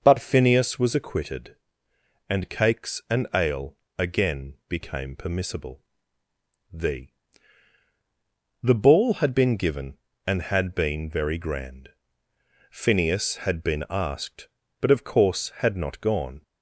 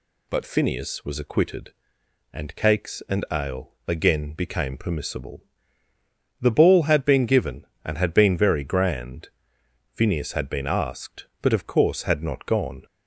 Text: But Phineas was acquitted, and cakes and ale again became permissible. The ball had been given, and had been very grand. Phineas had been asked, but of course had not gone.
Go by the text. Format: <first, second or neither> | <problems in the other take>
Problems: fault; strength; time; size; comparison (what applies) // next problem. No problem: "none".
second | pauses between "ale" and "again"; slight; at 3.7 s; 0.20 s long // says "The" twice; at 8.6 s